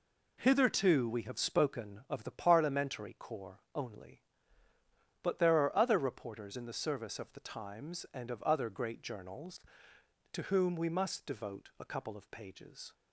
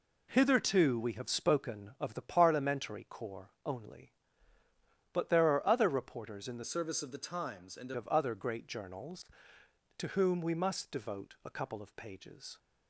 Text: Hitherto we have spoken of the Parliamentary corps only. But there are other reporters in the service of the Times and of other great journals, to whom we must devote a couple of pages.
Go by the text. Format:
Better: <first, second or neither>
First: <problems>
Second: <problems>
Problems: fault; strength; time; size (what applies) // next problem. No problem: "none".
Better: first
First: pauses between "corps" and "only"; slight; at 3.5 s; 0.16 s long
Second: pauses between "corps" and "only"; slight; at 3.4 s; 0.16 s long // changes voice from "service" to "and"; from 6.6 to 7.9 s; 1.3 s long